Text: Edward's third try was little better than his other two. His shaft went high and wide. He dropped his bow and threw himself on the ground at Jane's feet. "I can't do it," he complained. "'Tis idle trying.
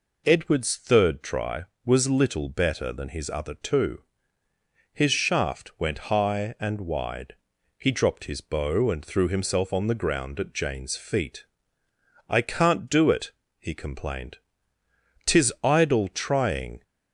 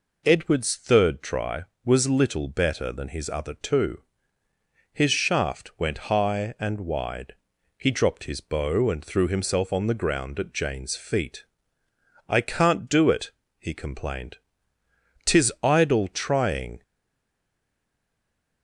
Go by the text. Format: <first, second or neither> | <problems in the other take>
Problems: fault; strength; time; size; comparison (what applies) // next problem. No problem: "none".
first | stays silent after the last word; noticeable; from 16.8 s on; 1.8 s long